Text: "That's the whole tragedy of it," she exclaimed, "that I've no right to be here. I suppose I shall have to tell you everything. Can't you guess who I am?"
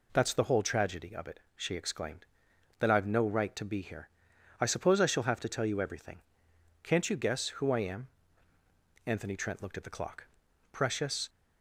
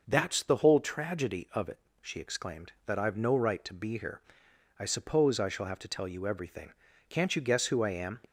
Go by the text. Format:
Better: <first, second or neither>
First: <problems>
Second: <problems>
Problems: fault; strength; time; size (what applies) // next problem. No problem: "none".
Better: second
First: goes on to say "Anthony Trent looked at the clock Precious"; strong; from 9.0 s on; 2.2 s long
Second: none